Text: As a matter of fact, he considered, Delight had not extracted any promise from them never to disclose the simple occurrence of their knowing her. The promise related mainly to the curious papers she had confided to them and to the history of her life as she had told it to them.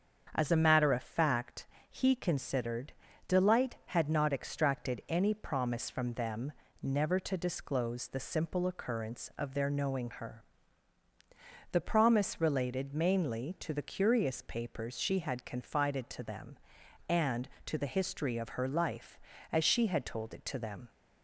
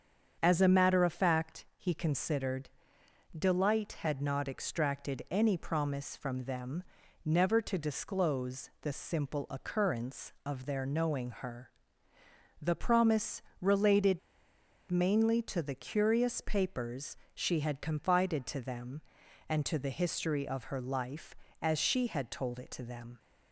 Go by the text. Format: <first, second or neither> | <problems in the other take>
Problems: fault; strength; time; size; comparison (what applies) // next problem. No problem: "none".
first | starts louder than the rest; strong; until 1.4 s; 7 dB; strong in the first // pauses between "them" and "never"; at 6.8 s; 0.42 s long; slight in the first // pauses between "promise" and "related"; slight; at 13.4 s; 0.18 s long // pauses between "related" and "mainly"; noticeable; at 14.2 s; 0.70 s long // pauses between "papers" and "she"; slight; at 17.1 s; 0.16 s long